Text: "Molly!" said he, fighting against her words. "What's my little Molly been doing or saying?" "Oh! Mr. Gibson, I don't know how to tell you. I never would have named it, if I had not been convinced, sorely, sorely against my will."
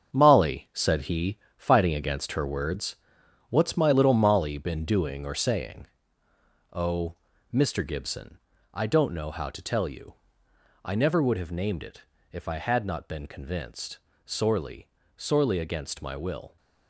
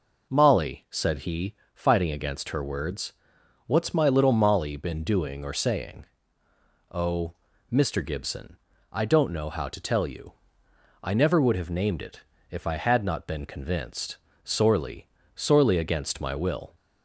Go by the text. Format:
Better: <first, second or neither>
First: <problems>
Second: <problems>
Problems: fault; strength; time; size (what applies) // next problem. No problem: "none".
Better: second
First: gets quieter; strong; throughout; 8 dB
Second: none